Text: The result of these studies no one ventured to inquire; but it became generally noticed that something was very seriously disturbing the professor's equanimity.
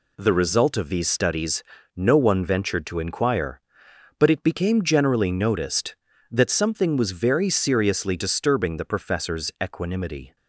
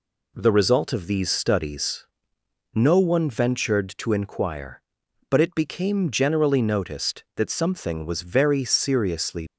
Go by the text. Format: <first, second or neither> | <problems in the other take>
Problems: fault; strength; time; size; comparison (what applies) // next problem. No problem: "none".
first | pauses between "studies" and "no"; noticeable; at 2.0 s; 0.68 s long; slight in the first // stops before "disturbing the professor's equanimity"; at 9.4 s